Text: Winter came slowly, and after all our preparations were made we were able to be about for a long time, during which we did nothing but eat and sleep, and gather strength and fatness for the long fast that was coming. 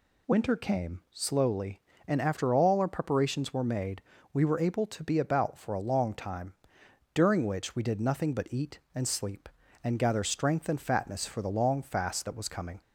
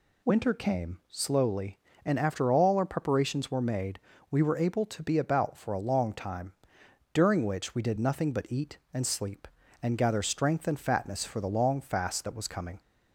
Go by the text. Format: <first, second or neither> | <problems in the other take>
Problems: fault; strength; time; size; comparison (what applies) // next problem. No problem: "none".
neither | pauses between "made" and "we"; slight; the same in both